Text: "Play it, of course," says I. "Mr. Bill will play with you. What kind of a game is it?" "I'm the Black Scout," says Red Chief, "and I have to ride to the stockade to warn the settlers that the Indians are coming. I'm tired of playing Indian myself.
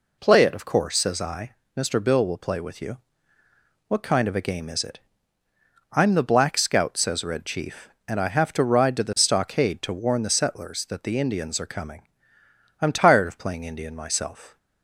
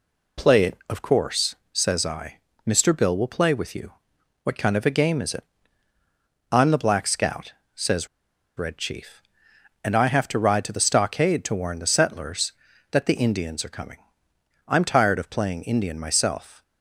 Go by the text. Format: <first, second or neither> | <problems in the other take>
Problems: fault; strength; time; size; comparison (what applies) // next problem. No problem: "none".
first | pauses between "says" and "Red"; noticeable; at 8.0 s; 0.50 s long